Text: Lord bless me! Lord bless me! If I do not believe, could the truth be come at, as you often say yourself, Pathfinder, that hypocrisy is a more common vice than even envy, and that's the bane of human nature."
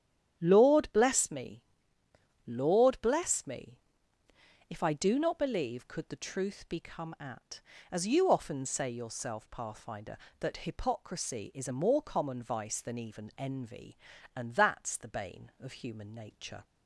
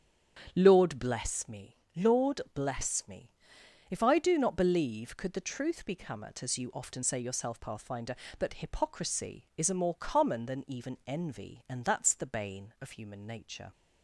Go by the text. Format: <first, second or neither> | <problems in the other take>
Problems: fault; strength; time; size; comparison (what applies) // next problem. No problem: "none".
first | starts louder than the rest; strong; until 1.5 s; 8.5 dB; strong in the first // skips "vice"; at 10.4 s